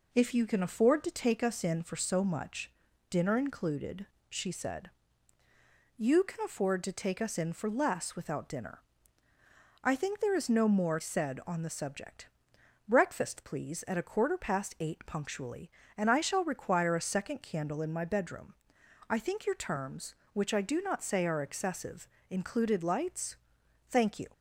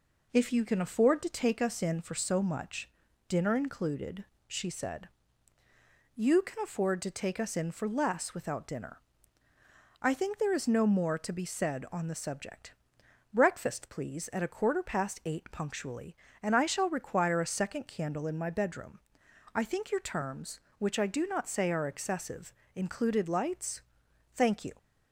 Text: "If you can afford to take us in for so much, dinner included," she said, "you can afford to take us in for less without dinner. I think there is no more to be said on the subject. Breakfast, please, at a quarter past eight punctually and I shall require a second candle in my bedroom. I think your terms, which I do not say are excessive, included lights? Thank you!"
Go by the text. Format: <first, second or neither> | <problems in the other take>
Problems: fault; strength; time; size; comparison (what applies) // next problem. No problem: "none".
second | skips "to be"; at 10.9 s